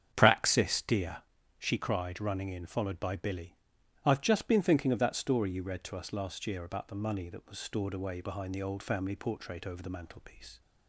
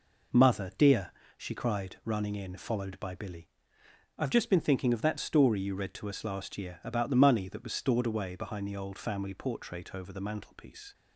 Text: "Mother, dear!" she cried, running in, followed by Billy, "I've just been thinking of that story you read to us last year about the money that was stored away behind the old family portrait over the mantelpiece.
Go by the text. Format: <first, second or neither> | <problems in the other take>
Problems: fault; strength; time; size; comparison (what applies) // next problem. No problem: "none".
second | starts louder than the rest; strong; until 1.1 s; 8 dB // says "Praxis" for "Mother"; at 0.1 s